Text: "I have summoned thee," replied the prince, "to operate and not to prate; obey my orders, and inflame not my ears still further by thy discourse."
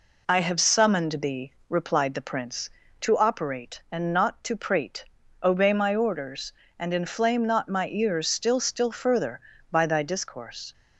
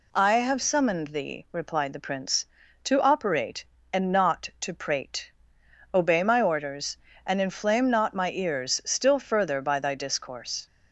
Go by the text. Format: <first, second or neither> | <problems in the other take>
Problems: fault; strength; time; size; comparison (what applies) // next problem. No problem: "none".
second | says "still" twice; at 8.5 s